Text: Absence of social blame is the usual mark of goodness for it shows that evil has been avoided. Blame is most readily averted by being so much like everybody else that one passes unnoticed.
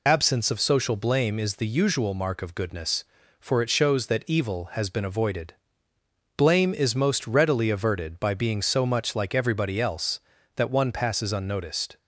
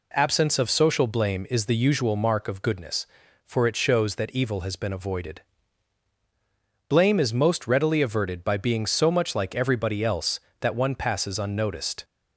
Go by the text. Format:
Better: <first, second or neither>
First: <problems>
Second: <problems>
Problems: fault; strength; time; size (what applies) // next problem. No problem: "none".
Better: second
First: loses the start of "Absence"; at 0.0 s; 45 ms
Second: none